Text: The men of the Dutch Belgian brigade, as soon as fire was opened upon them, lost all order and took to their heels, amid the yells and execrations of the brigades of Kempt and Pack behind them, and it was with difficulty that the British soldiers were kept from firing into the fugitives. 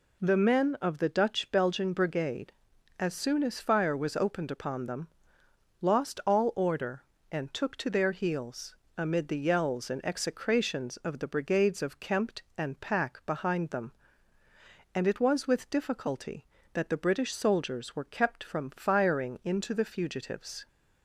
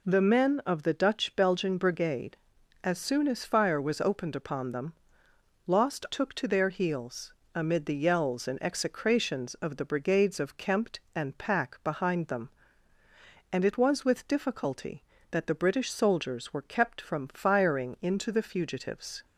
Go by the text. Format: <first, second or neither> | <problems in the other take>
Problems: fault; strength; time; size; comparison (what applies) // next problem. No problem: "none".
first | skips "all order and"; at 6.0 s